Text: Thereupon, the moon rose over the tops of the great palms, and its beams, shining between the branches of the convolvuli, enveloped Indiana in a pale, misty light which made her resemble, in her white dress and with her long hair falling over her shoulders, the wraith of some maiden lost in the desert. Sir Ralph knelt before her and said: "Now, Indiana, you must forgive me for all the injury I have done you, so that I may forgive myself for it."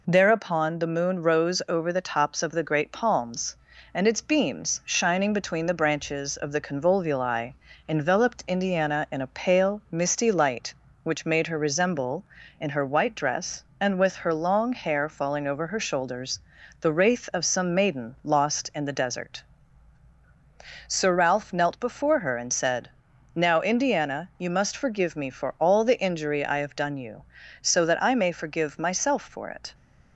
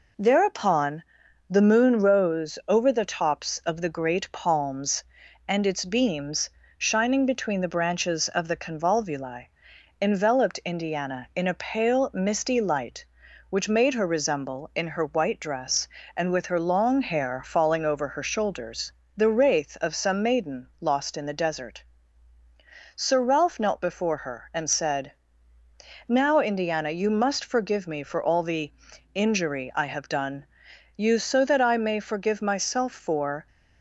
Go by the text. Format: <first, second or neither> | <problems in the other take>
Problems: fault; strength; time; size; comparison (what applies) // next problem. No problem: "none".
first | pauses between "the" and "injury"; at 28.7 s; 0.40 s long // pauses between "done" and "you"; noticeable; at 30.4 s; 0.50 s long // stops before "it"; at 33.4 s